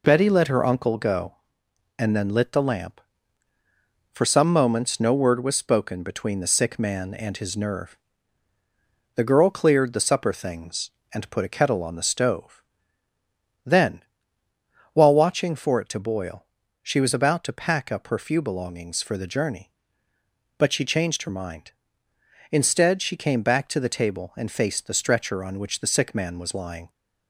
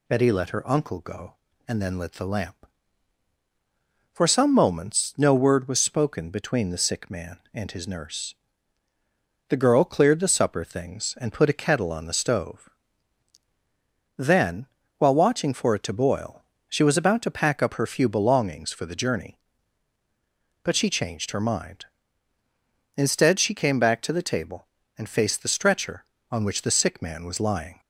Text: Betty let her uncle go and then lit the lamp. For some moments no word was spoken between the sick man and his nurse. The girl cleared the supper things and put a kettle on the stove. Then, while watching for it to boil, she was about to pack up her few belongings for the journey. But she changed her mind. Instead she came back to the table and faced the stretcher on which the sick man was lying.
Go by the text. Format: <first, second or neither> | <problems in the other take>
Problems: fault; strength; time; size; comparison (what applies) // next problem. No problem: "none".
second | says "nerve" for "nurse"; at 7.5 s